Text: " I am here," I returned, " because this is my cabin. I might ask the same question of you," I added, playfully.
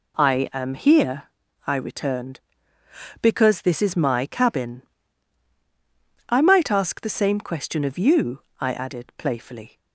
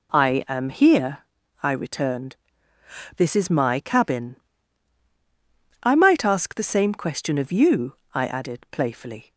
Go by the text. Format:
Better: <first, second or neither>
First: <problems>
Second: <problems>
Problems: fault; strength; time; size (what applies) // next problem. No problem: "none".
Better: first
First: none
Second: skips "because"; at 3.1 s